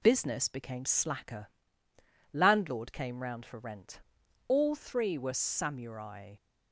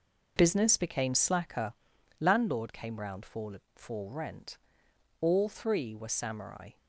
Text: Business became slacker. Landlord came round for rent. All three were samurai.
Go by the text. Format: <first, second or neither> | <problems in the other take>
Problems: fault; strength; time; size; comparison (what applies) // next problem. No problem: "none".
first | says "for" twice; at 3.7 s